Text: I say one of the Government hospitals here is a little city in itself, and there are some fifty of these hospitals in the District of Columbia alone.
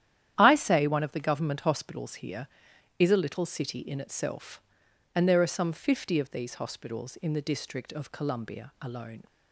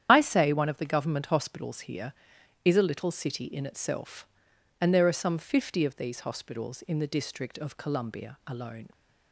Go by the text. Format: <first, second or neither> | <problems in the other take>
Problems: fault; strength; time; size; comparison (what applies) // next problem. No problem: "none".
first | loses the start of "I"; at 0.0 s; 65 ms // starts louder than the rest; strong; until 1.1 s; 9.5 dB; strong in the first